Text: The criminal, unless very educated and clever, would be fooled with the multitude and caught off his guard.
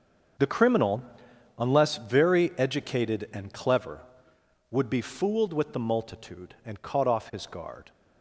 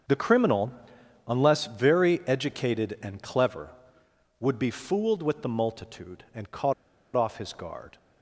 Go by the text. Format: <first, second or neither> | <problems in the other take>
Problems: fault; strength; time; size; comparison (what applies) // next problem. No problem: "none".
first | starts louder than the rest; until 1.6 s; 7 dB; also in the first // pauses between "caught" and "off"; at 6.7 s; 0.42 s long